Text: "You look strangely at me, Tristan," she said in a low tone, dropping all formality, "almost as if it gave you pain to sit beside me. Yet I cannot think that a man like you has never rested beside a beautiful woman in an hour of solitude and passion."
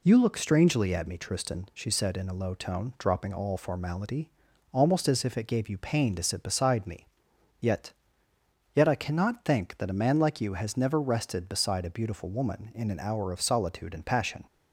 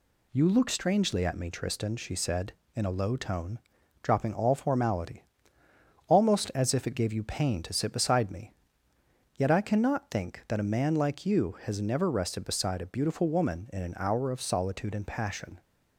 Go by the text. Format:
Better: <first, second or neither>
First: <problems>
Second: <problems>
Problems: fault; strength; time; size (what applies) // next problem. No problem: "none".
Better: second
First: says "Yet" twice; at 8.7 s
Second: none